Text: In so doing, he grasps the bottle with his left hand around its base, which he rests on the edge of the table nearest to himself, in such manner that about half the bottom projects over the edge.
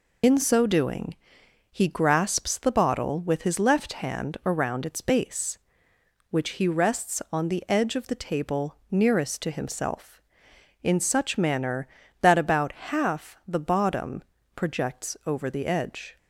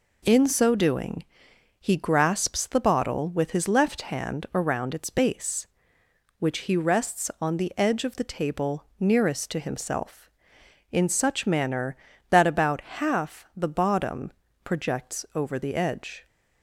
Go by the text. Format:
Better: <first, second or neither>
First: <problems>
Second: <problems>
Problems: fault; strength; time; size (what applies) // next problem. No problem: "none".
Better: second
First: loses the start of "In"; at 0.2 s; 90 ms // pauses between "bottom" and "projects"; slight; at 14.2 s; 0.32 s long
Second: pauses between "bottom" and "projects"; slight; at 14.3 s; 0.32 s long